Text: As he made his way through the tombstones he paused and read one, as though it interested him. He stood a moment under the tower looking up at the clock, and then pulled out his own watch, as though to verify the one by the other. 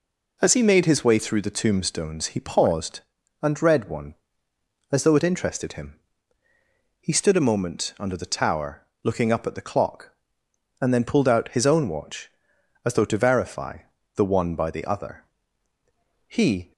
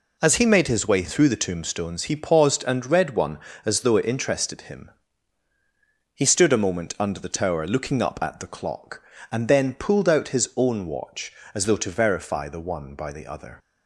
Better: second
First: pauses between "tower" and "looking"; slight; at 8.8 s; 0.22 s long // pauses between "verify" and "the"; at 13.7 s; 0.38 s long // goes on to say "He"; slight; from 16.2 s on; 0.46 s long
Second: none

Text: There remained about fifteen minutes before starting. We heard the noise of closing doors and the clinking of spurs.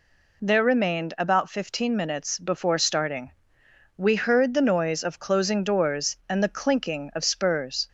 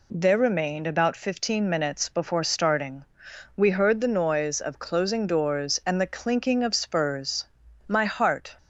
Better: first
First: none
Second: goes on to say "My heart"; noticeable; from 7.8 s on; 0.70 s long

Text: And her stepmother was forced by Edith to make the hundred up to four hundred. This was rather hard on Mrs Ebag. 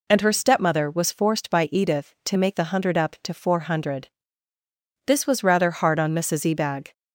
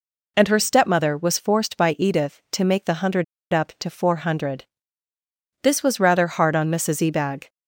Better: first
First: none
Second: pauses between "hundred" and "up"; slight; at 3.2 s; 0.28 s long

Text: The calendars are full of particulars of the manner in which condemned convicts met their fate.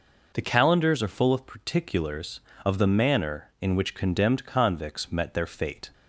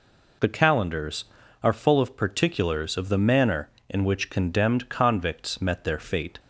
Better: neither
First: none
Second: none

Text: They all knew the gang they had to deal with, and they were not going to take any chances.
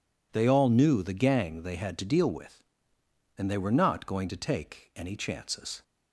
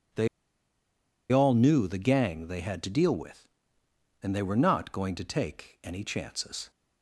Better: first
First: none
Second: pauses between "They" and "all"; at 0.2 s; 1.0 s long

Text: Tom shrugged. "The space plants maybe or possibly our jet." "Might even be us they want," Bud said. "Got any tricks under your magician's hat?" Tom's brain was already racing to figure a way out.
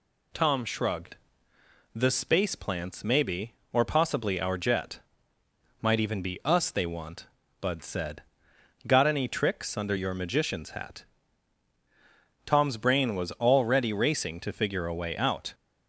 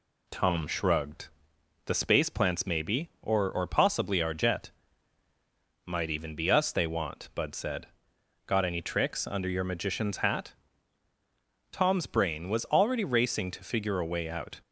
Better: first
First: none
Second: says "or" twice; at 3.4 s

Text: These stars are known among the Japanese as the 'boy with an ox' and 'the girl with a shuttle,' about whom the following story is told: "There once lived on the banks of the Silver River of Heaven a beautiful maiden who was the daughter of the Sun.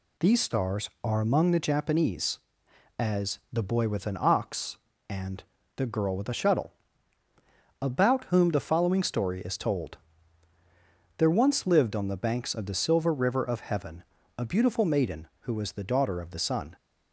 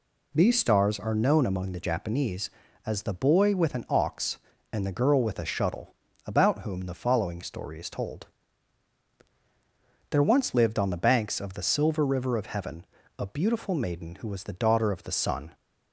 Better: second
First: skips "known"; at 1.2 s // pauses between "and" and "the"; slight; at 5.4 s; 0.32 s long // pauses between "Heaven" and "a"; slight; at 14.0 s; 0.34 s long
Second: pauses between "Heaven" and "a"; slight; at 12.8 s; 0.36 s long

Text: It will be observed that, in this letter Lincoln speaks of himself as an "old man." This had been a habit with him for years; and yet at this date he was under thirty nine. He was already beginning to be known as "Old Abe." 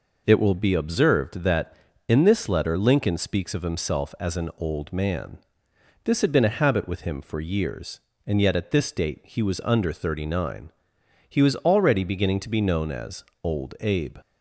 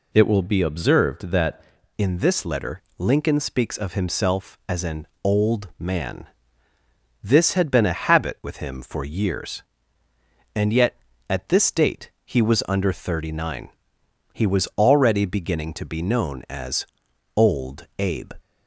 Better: first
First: pauses between "as" and "Old"; slight; at 13.2 s; 0.20 s long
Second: changes voice at "in"; from 1.9 s on; 16.4 s long // pauses between "letter" and "Lincoln"; slight; at 2.8 s; 0.16 s long // pauses between "an" and "old"; slight; at 5.0 s; 0.16 s long // pauses between "as" and "Old"; noticeable; at 16.8 s; 0.50 s long

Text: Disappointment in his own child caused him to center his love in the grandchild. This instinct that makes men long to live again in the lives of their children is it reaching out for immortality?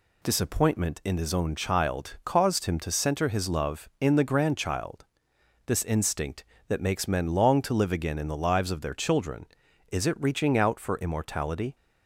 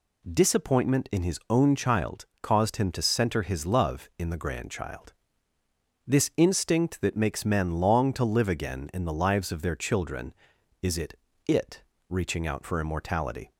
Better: first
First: none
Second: pauses between "child" and "caused"; slight; at 2.2 s; 0.16 s long // says "it" twice; at 11.4 s

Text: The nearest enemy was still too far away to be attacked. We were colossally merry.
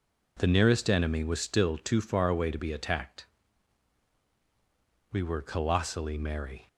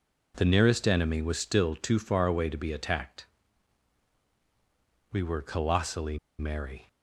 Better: first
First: none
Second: pauses between "colossally" and "merry"; slight; at 6.1 s; 0.21 s long

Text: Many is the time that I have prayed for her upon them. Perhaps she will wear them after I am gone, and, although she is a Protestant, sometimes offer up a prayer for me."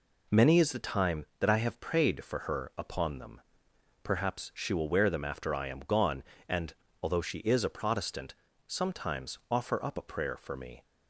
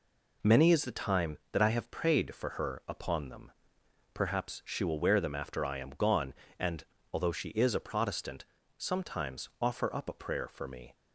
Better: neither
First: none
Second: none

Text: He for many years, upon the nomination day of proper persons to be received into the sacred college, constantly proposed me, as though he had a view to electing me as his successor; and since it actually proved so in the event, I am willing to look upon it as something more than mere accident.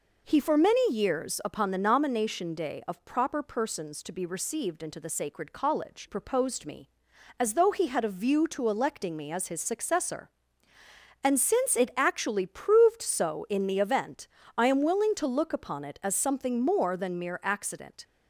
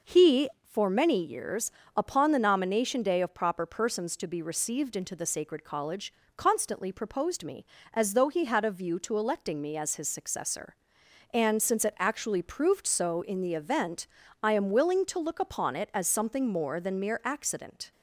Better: second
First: skips "constantly"; at 6.0 s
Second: none

